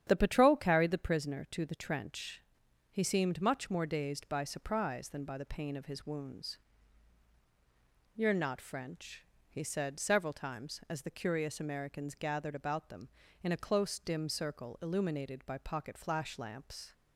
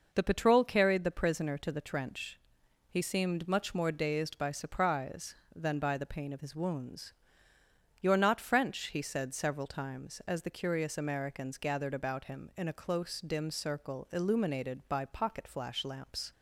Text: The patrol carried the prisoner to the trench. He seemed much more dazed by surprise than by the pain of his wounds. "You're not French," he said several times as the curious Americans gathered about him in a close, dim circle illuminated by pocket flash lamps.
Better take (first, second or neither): second